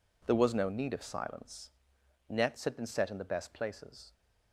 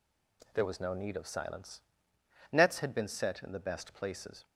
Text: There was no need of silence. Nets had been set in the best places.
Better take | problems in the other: neither | none

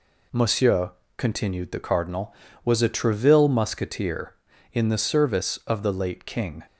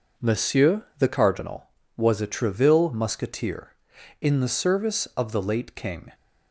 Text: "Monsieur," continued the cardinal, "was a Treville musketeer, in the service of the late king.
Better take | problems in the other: first | skips "continued"; at 0.9 s

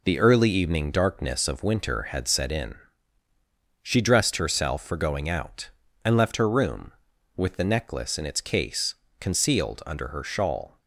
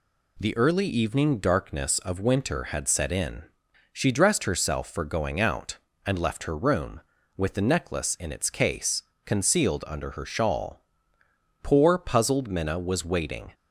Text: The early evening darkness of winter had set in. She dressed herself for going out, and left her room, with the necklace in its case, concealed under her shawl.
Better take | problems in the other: first | goes on to say "Poor puzzled Minna was waiting"; strong; from 11.6 s on; 1.8 s long

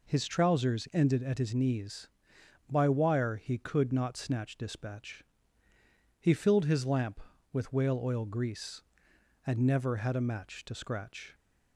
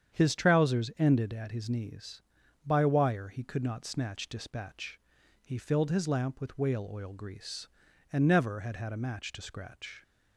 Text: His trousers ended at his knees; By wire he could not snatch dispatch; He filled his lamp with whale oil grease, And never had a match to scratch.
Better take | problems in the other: first | starts louder than the rest; strong; until 1.2 s; 8 dB // says "had" twice; at 8.7 s

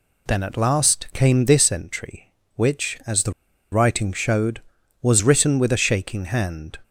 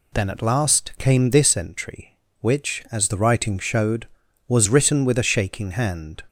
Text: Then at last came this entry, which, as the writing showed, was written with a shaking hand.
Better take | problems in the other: second | pauses between "the" and "writing"; at 3.3 s; 0.39 s long

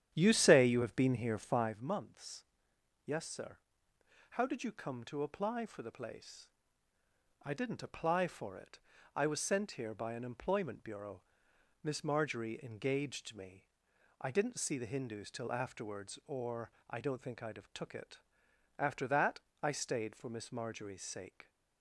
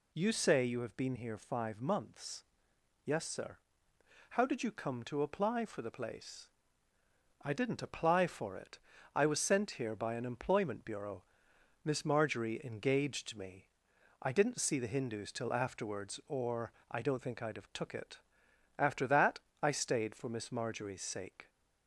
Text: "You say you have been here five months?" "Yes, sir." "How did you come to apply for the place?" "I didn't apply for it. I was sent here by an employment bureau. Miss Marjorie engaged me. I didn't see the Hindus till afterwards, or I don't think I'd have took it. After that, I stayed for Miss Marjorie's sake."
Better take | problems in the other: second | starts louder than the rest; strong; until 1.8 s; 10 dB // pauses between "or" and "I"; slight; at 16.7 s; 0.18 s long; slight in the second

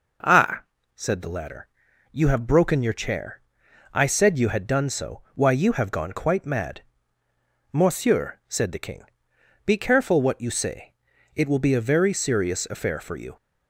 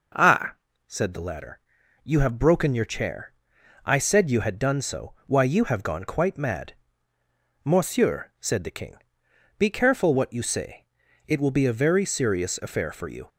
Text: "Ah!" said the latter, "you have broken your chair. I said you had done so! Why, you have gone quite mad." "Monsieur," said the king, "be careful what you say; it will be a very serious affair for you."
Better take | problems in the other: neither | none

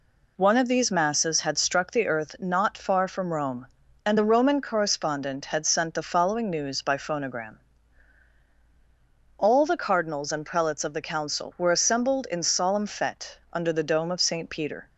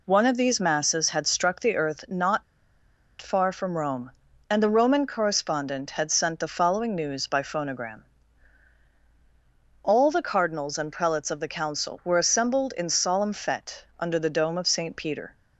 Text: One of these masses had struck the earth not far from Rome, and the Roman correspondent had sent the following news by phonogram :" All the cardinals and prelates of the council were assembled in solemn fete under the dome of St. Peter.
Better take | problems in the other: first | pauses between "not" and "far"; noticeable; at 2.4 s; 0.77 s long

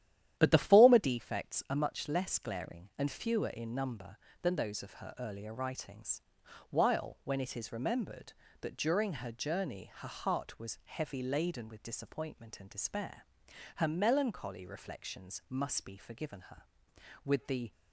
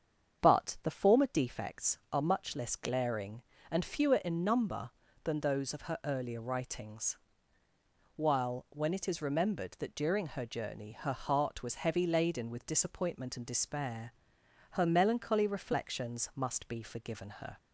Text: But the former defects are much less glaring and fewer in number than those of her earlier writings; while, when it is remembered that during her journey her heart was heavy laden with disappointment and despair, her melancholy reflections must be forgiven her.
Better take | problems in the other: second | starts louder than the rest; strong; until 1.3 s; 11 dB; strong in the second // goes on to say "With the"; slight; from 17.2 s on; 0.48 s long

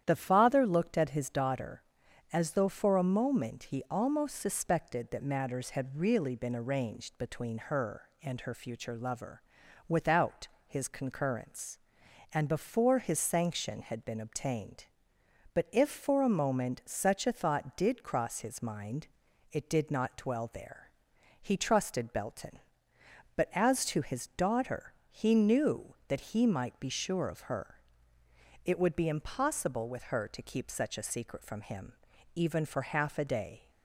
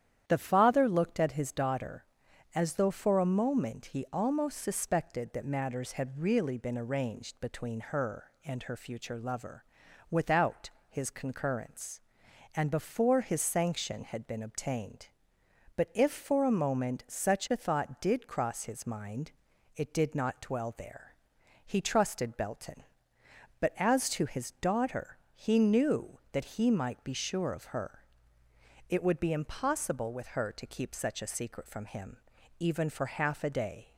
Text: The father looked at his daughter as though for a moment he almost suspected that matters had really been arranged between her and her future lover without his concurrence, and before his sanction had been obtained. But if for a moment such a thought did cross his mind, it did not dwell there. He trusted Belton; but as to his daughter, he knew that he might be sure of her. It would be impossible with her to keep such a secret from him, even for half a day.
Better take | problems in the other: neither | starts louder than the rest; strong; the same in both // pauses between "lover" and "without"; noticeable; the same in both // pauses between "without" and "his"; slight; the same in both

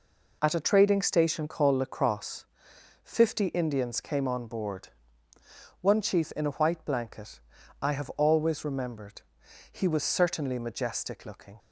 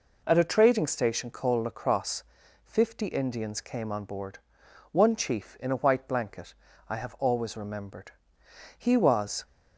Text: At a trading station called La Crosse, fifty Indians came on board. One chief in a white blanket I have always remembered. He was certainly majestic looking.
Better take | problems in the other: first | pauses between "blanket" and "I"; slight; at 6.5 s; 0.34 s long; also in the first // stops before "certainly majestic looking"; at 9.4 s

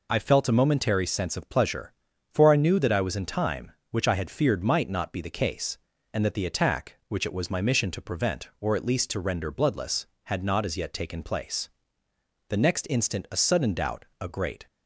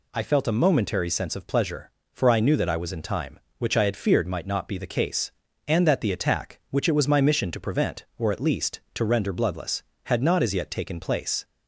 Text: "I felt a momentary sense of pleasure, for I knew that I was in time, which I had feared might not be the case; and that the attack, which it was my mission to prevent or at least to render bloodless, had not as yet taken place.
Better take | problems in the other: second | goes on to say "The next instant a sudden doubt a great"; strong; from 12.4 s on; 2.1 s long

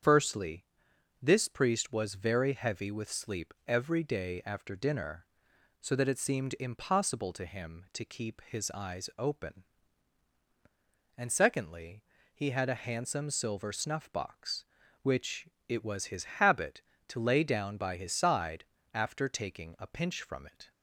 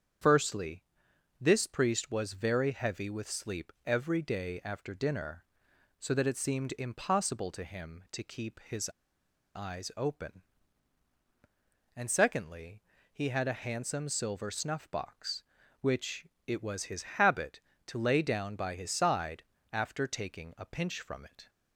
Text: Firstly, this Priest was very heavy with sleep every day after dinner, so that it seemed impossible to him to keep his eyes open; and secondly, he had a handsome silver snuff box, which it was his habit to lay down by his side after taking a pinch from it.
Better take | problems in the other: first | starts louder than the rest; strong; until 1.7 s; 7.5 dB; strong in the first // pauses between "his" and "eyes"; noticeable; at 8.8 s; 0.66 s long // pauses between "which" and "it"; slight; at 16.2 s; 0.18 s long; slight in the first // pauses between "his" and "habit"; slight; at 17.0 s; 0.16 s long; slight in the first // pauses between "side" and "after"; slight; at 19.4 s; 0.32 s long; slight in the first

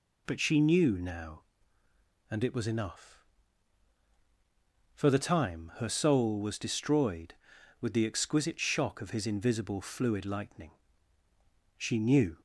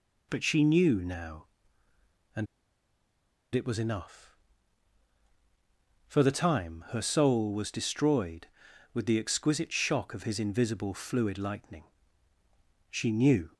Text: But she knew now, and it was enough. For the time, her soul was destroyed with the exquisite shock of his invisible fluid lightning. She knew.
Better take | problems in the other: first | pauses between "and" and "it"; at 2.4 s; 1.0 s long

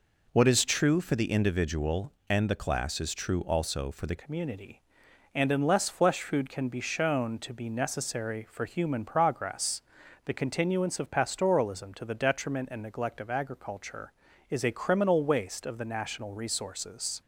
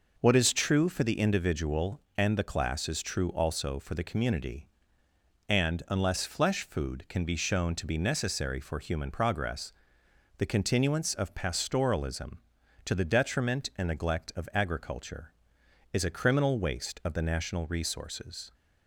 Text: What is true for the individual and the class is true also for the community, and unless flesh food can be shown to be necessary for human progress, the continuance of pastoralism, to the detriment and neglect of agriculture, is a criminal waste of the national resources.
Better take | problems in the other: second | changes voice at "community"; from 4.1 s on; 13.1 s long

